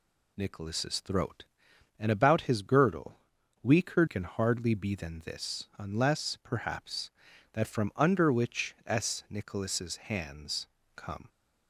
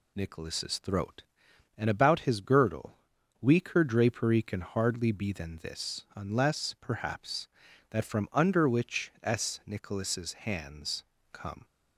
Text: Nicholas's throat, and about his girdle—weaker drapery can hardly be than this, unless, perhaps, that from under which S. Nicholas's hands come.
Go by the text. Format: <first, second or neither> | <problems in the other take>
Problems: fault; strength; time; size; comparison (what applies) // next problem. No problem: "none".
second | skips "drapery"; at 4.0 s // pauses between "hands" and "come"; slight; at 10.6 s; 0.30 s long; slight in the second